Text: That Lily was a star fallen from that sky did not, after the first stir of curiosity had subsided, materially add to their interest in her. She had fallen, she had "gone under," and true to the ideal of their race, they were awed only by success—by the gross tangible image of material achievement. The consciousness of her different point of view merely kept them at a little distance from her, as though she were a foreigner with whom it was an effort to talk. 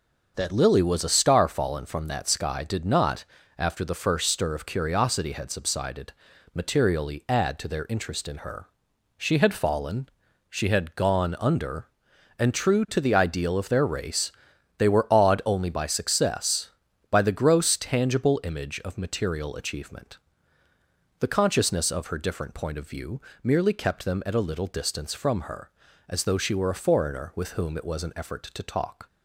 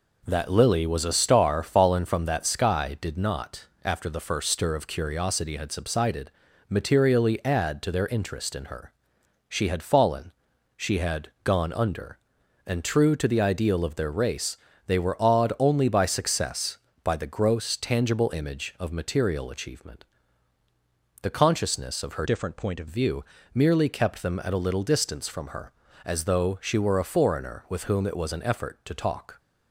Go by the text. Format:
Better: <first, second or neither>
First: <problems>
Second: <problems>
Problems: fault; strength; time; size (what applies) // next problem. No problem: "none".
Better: first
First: pauses between "view" and "merely"; slight; at 23.2 s; 0.22 s long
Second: changes voice from "different" to "of"; from 22.2 to 22.8 s; 0.6 s long // pauses between "view" and "merely"; slight; at 23.2 s; 0.30 s long